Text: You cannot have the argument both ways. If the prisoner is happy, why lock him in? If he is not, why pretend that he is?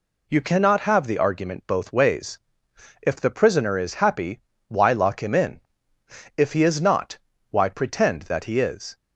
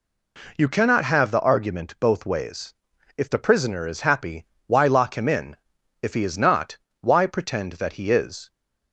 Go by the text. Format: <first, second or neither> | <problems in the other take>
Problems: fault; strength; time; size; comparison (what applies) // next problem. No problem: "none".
neither | none